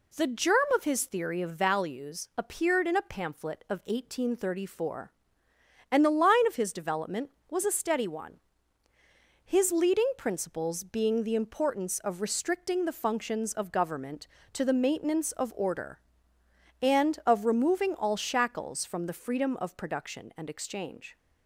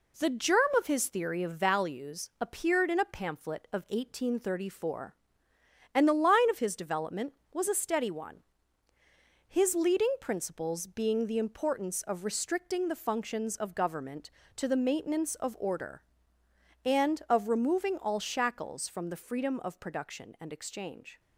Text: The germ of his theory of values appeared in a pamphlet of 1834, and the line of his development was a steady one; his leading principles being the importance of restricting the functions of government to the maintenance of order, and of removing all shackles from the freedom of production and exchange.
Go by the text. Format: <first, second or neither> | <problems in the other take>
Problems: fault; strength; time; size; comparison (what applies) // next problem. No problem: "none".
first | gets quieter; noticeable; throughout; 4 dB